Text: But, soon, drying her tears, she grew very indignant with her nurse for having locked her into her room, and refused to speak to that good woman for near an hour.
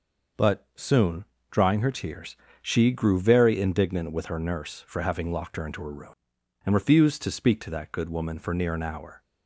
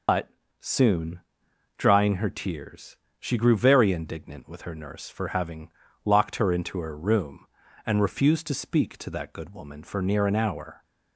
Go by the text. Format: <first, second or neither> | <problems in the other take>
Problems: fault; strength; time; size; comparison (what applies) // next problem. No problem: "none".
first | loses the start of "But"; at 0.0 s; 115 ms // pauses between "having" and "locked"; slight; at 5.7 s; 0.32 s long